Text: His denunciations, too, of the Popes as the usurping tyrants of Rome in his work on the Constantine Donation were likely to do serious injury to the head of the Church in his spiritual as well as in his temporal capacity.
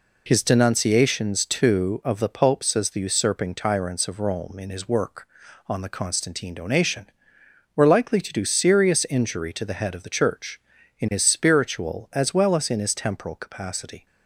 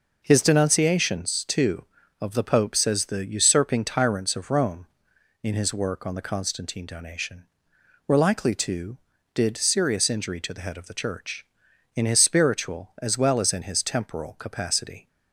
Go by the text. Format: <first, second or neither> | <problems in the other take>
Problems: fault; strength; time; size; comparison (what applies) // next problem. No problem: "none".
first | says "did" for "do"; at 9.3 s